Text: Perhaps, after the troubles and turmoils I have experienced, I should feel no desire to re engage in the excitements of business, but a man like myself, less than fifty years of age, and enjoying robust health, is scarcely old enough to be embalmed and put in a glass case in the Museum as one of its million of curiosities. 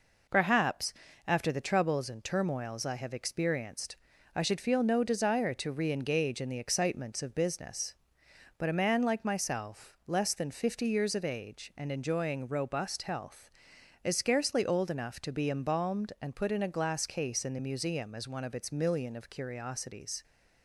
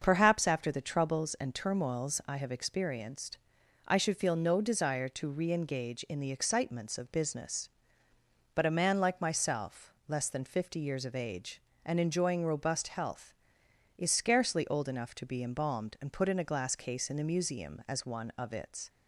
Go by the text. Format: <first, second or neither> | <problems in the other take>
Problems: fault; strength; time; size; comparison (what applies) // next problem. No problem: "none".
first | starts louder than the rest; until 1.0 s; 6.5 dB // stops before "million of curiosities"; at 18.8 s